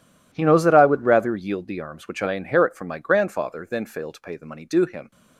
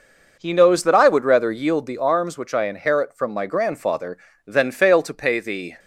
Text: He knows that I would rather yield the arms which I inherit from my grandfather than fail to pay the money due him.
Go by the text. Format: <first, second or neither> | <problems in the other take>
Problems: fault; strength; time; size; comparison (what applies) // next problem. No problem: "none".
first | stops before "money due him"; at 5.7 s